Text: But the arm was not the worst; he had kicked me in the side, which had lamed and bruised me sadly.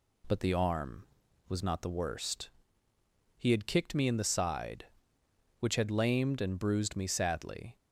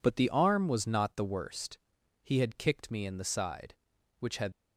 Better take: first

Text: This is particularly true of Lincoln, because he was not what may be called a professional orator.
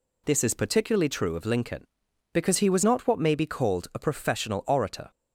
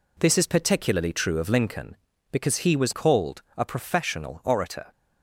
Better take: first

